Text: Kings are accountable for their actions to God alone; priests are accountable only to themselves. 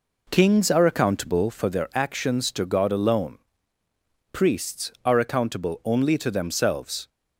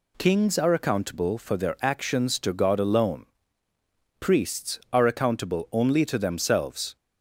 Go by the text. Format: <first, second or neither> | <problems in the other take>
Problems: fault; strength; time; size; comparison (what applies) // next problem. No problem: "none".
second | starts louder than the rest; noticeable; until 1.8 s; 4 dB